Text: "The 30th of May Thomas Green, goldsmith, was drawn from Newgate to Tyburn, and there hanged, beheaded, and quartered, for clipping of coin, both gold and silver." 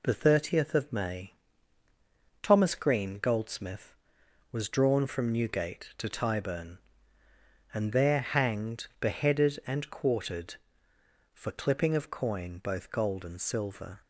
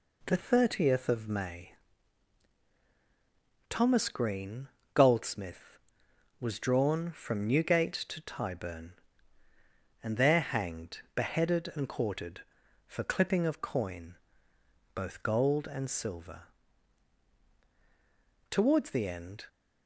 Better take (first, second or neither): first